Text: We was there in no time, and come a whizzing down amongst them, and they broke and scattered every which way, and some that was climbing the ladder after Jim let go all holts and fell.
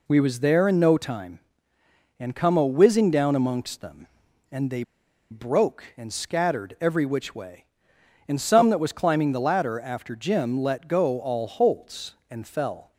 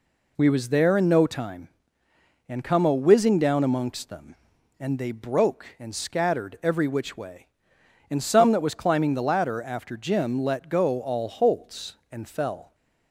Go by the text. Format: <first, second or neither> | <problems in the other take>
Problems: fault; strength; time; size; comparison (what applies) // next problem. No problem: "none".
second | pauses between "they" and "broke"; noticeable; at 4.8 s; 0.47 s long